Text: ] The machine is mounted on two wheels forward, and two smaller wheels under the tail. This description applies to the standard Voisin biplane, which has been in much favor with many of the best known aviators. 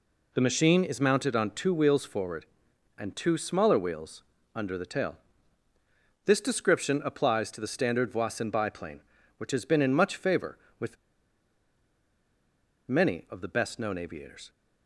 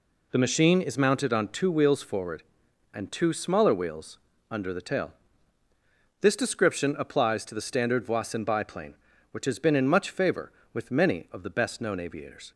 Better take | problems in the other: second | pauses between "wheels" and "under"; slight; at 4.2 s; 0.32 s long; slight in the second // pauses between "with" and "many"; strong; at 10.9 s; 1.9 s long

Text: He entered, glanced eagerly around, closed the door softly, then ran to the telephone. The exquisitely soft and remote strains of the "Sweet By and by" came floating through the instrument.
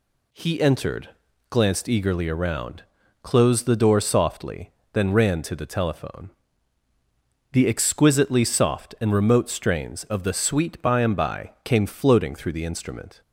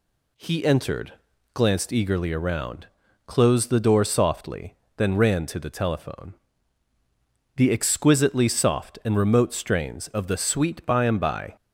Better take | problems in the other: first | stops before "came floating through the instrument"; at 11.5 s

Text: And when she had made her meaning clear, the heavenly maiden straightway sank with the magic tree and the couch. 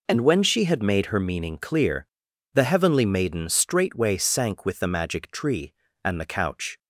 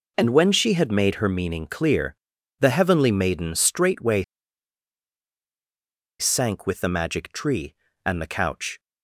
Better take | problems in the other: first | pauses between "straightway" and "sank"; strong; at 4.2 s; 1.9 s long

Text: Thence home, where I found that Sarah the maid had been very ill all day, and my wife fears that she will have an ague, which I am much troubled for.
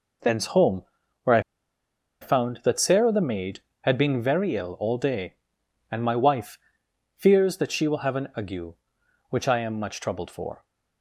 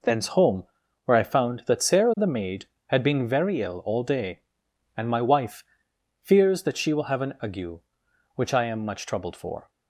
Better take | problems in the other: second | pauses between "I" and "found"; noticeable; at 1.3 s; 0.81 s long // pauses between "wife" and "fears"; noticeable; at 6.5 s; 0.56 s long; noticeable in the second

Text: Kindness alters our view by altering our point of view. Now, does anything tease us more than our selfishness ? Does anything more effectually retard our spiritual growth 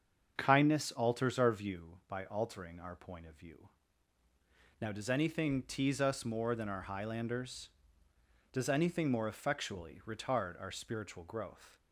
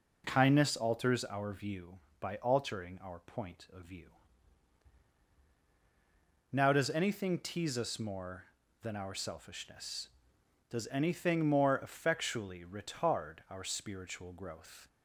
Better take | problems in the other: second | starts louder than the rest; until 1.3 s; 7 dB // says "highlanders" for "selfishness"; at 6.8 s

